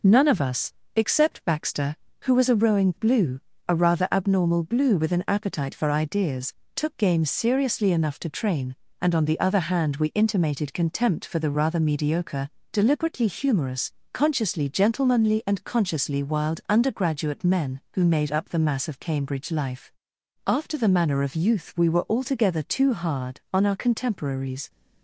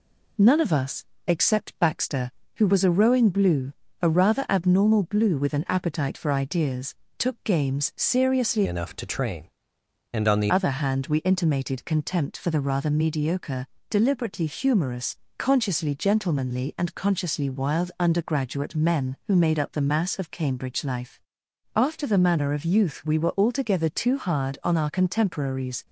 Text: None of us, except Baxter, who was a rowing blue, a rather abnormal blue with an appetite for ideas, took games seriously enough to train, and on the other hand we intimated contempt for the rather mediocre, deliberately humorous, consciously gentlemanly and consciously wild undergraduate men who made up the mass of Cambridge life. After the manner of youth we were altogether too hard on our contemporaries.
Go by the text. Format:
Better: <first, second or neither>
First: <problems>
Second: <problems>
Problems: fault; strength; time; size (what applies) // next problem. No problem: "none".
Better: first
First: none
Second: changes voice from "enough" to "the"; from 8.6 to 10.5 s; 1.9 s long